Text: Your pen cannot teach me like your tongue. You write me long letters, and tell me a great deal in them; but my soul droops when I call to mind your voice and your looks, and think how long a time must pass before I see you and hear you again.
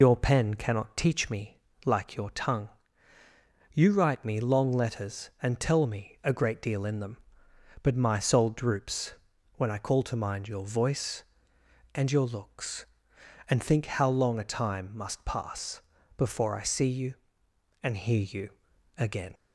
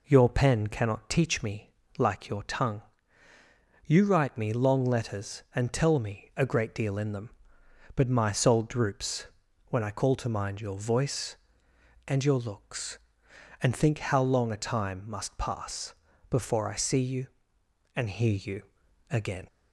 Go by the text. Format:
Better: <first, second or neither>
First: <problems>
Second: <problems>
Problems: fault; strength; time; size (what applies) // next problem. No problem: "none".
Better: second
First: loses the start of "Your"; at 0.0 s; 70 ms // pauses between "me" and "like"; slight; at 1.5 s; 0.28 s long // pauses between "droops" and "when"; at 9.1 s; 0.42 s long // pauses between "pass" and "before"; slight; at 15.8 s; 0.36 s long // pauses between "you" and "again"; noticeable; at 18.4 s; 0.46 s long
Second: pauses between "me" and "like"; slight; at 1.7 s; 0.28 s long // pauses between "droops" and "when"; at 9.2 s; 0.42 s long // pauses between "pass" and "before"; slight; at 15.9 s; 0.36 s long // pauses between "you" and "again"; noticeable; at 18.6 s; 0.46 s long